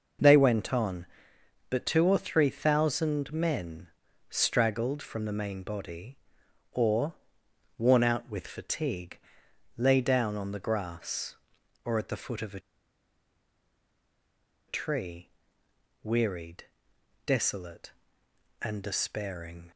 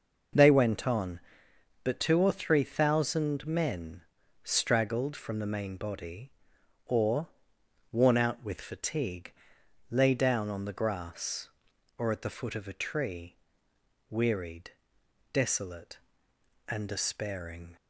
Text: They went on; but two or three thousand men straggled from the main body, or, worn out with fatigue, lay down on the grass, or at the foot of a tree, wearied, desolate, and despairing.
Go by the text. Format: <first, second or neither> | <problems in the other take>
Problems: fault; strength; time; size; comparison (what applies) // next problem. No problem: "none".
second | pauses between "men" and "straggled"; at 3.8 s; 0.40 s long; also in the second // pauses between "a" and "tree"; strong; at 12.6 s; 2.0 s long